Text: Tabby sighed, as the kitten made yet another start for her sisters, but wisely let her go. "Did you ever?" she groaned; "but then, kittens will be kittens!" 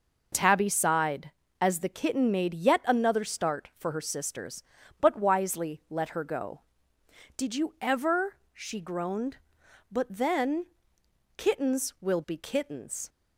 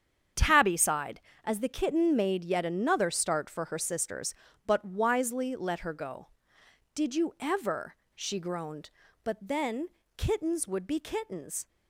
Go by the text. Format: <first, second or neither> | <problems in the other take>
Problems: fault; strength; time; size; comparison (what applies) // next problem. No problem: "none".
first | starts louder than the rest; strong; until 1.6 s; 8 dB // says "would" for "will"; at 10.6 s